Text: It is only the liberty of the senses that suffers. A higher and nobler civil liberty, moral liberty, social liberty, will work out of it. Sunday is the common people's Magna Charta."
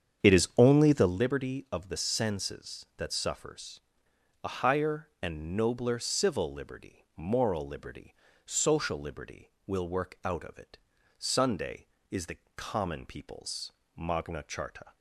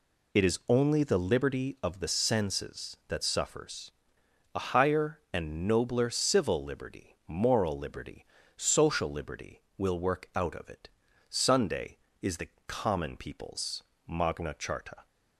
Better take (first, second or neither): second